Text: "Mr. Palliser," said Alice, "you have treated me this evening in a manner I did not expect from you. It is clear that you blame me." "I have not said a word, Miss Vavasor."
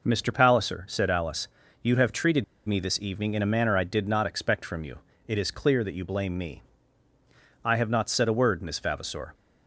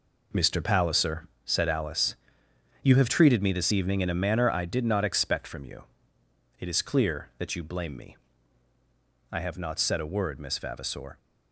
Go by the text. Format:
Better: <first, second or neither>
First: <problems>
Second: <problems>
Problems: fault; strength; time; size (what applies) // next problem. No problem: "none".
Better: second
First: pauses between "treated" and "me"; slight; at 2.4 s; 0.23 s long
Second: none